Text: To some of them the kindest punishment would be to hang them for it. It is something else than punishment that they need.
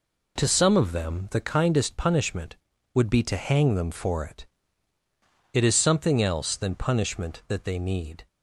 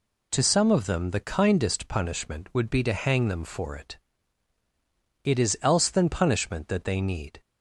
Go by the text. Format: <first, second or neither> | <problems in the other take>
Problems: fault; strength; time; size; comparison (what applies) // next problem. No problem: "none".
first | skips "something"; at 5.5 s